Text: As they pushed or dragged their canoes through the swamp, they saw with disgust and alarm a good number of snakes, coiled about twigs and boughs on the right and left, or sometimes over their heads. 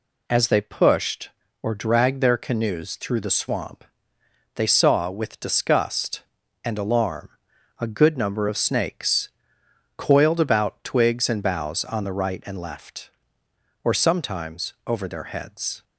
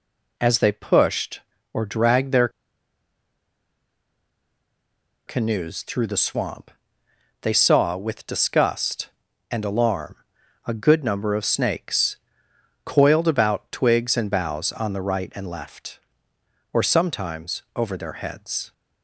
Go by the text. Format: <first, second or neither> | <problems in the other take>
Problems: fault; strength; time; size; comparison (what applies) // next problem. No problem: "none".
first | pauses between "their" and "canoes"; strong; at 2.4 s; 2.7 s long // pauses between "alarm" and "a"; noticeable; at 10.1 s; 0.50 s long; noticeable in the first // pauses between "sometimes" and "over"; slight; at 17.6 s; 0.16 s long; slight in the first